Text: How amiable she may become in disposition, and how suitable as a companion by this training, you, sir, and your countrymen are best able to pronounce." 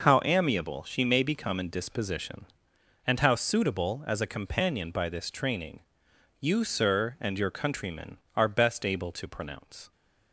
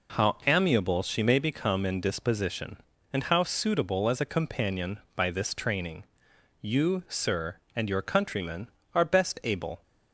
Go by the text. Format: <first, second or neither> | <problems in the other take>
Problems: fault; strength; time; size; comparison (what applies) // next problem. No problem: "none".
first | stops before "to pronounce"; at 9.8 s